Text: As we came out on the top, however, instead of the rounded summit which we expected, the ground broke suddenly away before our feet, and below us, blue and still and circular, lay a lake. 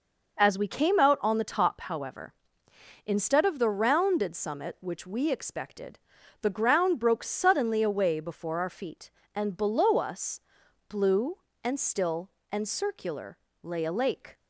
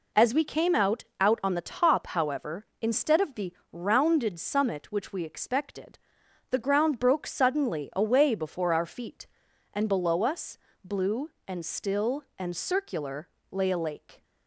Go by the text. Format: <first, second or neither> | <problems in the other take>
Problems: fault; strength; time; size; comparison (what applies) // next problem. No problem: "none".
first | says "out" twice; at 1.2 s // pauses between "the" and "rounded"; slight; at 3.5 s; 0.20 s long